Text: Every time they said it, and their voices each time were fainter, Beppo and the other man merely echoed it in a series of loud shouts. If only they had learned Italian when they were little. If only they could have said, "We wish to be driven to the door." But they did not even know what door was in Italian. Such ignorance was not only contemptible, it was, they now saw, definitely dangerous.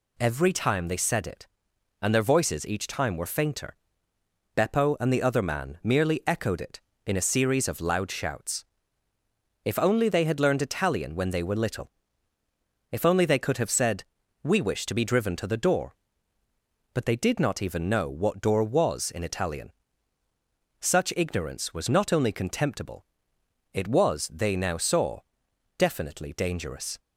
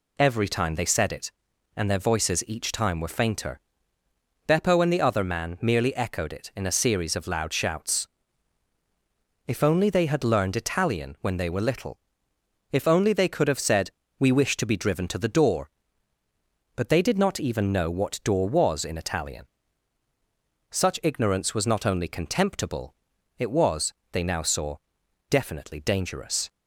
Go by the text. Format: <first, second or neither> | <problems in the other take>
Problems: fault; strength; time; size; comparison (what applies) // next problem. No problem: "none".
neither | none